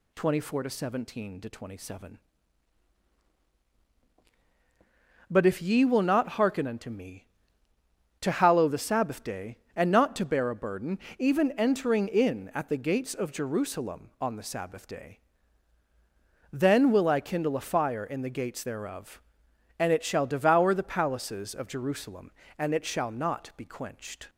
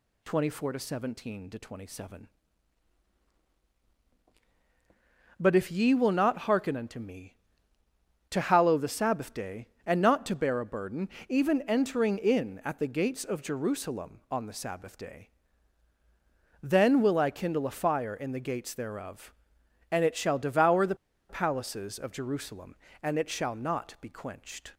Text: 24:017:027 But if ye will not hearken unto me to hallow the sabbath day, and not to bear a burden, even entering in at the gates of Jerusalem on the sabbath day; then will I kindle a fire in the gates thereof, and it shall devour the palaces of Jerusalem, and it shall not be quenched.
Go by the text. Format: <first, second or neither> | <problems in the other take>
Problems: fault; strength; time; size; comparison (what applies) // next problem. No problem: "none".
first | pauses between "the" and "palaces"; slight; at 20.9 s; 0.34 s long